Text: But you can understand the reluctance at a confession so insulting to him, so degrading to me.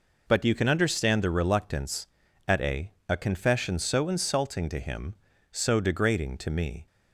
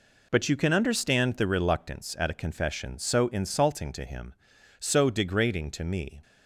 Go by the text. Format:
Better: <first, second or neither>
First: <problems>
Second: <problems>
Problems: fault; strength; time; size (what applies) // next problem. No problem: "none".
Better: second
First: says "a" twice; at 3.0 s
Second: none